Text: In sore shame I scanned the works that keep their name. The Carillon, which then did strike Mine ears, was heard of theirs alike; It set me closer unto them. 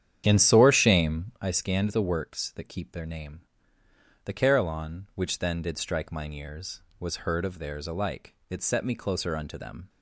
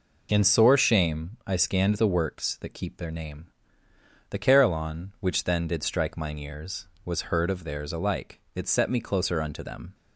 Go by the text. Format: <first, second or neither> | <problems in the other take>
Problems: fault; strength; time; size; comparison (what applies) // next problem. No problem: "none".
second | starts louder than the rest; strong; until 1.5 s; 9.5 dB